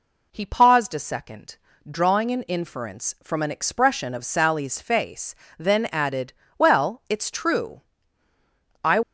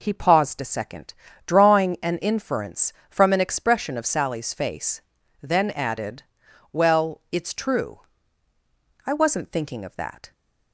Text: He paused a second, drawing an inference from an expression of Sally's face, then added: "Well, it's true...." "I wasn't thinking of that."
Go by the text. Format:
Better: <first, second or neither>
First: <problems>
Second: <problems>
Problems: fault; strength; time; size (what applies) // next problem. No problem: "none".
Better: second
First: stops before "wasn't thinking of that"; at 9.0 s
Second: none